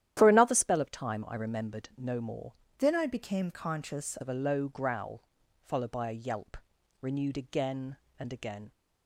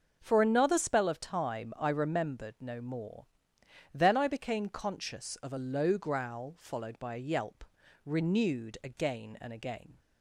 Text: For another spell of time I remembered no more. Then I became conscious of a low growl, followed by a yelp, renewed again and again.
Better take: second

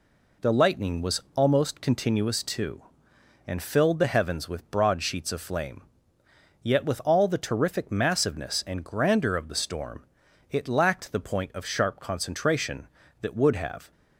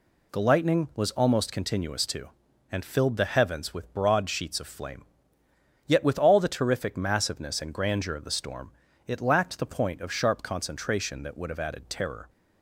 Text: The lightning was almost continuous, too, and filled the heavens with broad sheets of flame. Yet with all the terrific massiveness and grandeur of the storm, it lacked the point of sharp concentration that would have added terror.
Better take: second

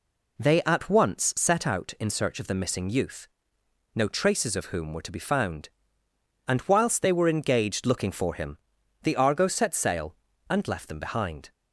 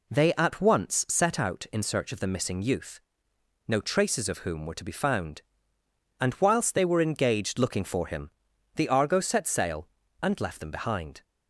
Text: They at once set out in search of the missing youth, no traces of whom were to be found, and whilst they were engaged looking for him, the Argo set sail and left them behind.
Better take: neither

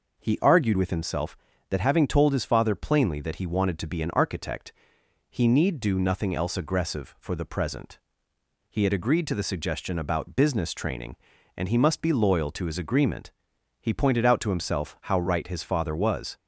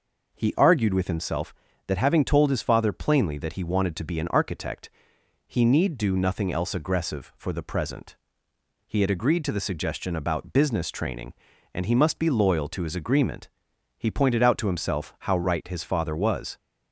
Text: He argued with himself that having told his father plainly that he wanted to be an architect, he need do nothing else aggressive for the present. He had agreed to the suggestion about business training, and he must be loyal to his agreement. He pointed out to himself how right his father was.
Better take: neither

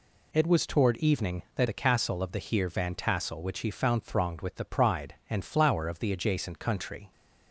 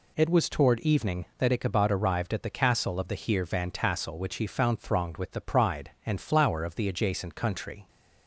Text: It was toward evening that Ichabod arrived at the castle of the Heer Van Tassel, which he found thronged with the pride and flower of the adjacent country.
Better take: second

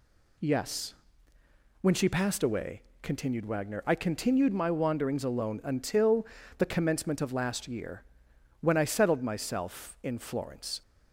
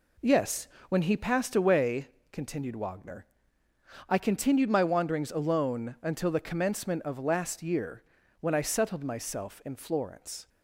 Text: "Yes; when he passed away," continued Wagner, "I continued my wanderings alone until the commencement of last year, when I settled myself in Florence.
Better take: second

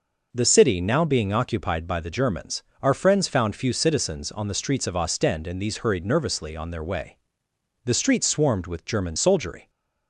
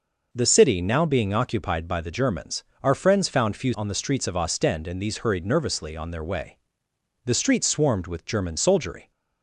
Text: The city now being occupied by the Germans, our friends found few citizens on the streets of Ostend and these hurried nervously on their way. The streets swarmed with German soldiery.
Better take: first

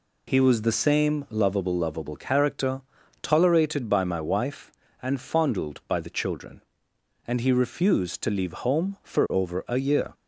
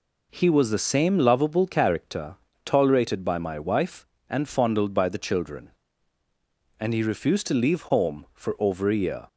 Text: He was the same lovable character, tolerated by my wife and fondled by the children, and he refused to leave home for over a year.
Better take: second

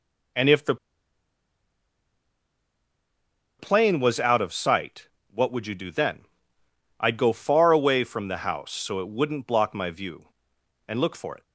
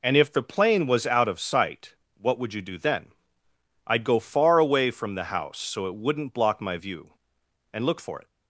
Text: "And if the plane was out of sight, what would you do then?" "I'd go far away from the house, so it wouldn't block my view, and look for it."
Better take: second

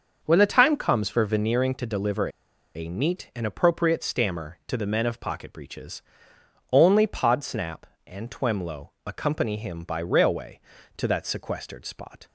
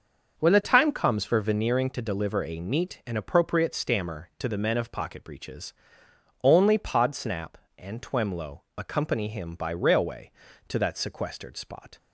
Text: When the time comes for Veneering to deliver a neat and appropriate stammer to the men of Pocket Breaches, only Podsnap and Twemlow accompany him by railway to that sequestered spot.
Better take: second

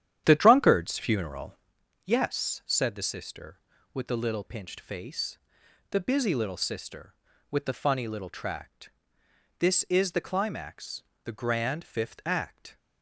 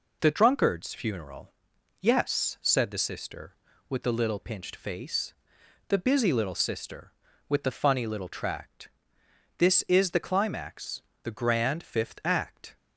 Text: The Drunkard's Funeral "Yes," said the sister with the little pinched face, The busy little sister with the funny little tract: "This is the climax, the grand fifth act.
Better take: second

